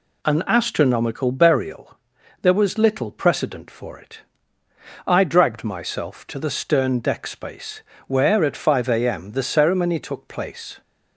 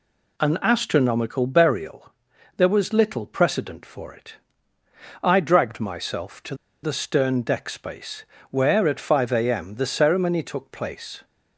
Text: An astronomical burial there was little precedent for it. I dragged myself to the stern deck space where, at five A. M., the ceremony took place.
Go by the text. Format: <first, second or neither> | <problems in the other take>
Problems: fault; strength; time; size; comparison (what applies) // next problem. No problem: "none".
first | pauses between "burial" and "there"; noticeable; at 2.1 s; 0.46 s long; noticeable in the first // pauses between "to" and "the"; slight; at 6.5 s; 0.29 s long // pauses between "space" and "where"; slight; at 8.2 s; 0.28 s long; slight in the first